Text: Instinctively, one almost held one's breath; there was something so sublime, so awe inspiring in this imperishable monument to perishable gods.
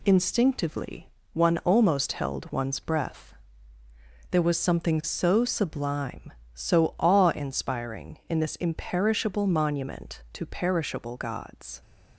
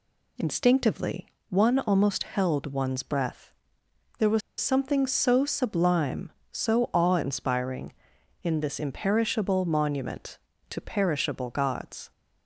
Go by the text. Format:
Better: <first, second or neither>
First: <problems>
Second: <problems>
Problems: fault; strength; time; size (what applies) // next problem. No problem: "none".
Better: first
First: none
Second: pauses between "was" and "something"; slight; at 4.4 s; 0.20 s long